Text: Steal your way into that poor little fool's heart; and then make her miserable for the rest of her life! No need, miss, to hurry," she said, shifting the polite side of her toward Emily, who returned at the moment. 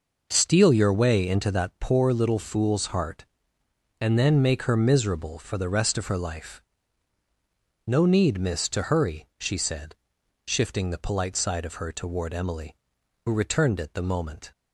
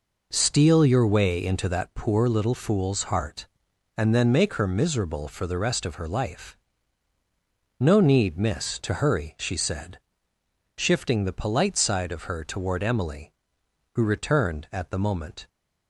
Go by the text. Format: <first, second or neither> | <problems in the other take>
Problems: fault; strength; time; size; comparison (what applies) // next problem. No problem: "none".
second | says "it" for "at"; at 13.7 s